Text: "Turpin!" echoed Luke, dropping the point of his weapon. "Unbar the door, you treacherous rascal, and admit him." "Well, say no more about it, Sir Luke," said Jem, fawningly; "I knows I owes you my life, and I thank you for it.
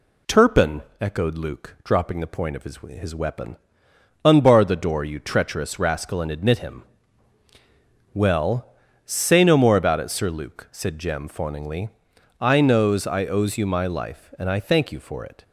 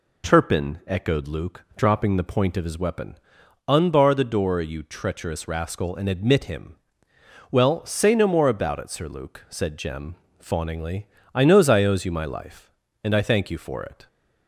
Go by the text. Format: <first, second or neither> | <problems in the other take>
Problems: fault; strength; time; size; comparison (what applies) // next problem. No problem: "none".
second | says "his" twice; at 2.7 s